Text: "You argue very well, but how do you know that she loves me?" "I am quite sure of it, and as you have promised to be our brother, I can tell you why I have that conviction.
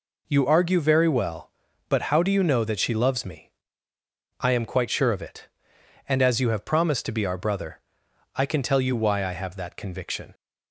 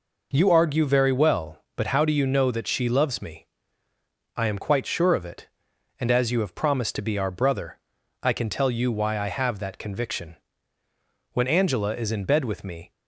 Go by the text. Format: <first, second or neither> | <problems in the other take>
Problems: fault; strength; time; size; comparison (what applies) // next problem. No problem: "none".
first | goes on to say "When Angela is in bed with me"; from 11.3 s on; 1.5 s long